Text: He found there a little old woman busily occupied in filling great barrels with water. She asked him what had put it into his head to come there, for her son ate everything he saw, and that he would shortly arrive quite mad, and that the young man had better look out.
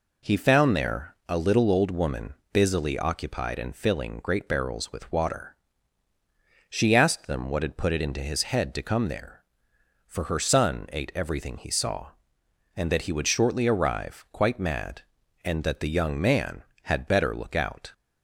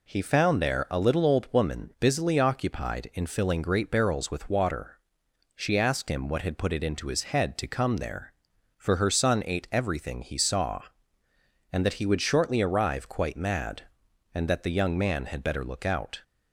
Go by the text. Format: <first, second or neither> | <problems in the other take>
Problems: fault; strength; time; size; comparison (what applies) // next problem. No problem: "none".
second | pauses between "woman" and "busily"; slight; at 2.3 s; 0.22 s long // says "them" for "him"; at 7.2 s